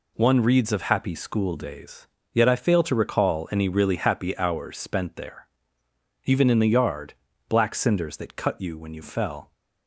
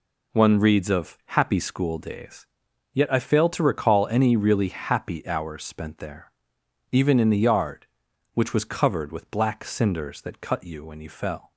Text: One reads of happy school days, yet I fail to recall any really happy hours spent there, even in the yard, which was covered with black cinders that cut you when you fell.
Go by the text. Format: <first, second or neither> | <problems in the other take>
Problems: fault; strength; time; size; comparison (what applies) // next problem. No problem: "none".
second | skips "which was covered with"; at 7.3 s